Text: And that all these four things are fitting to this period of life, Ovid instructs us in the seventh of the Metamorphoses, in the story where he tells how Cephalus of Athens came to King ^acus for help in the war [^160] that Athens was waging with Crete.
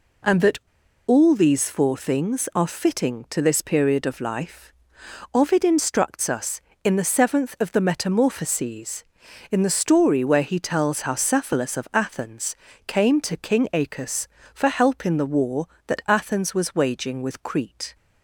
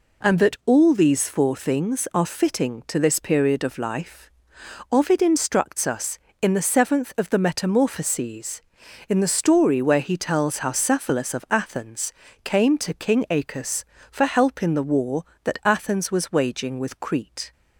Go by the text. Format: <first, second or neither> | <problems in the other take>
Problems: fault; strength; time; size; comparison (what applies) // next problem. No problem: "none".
second | pauses between "that" and "all"; noticeable; at 0.5 s; 0.49 s long // pauses between "Athens" and "came"; slight; at 12.5 s; 0.32 s long; slight in the second